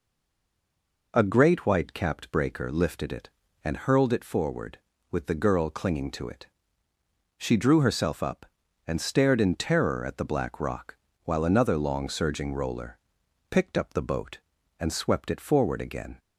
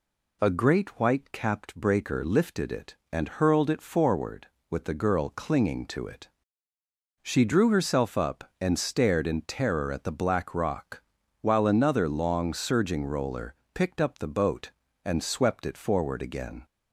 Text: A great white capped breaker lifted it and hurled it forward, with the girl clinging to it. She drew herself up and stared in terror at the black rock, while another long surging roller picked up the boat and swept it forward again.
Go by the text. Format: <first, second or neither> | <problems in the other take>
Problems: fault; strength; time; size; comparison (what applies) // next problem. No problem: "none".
second | stays silent before the first word; until 1.1 s; 1.1 s long // pauses between "roller" and "picked"; noticeable; at 12.9 s; 0.50 s long; slight in the second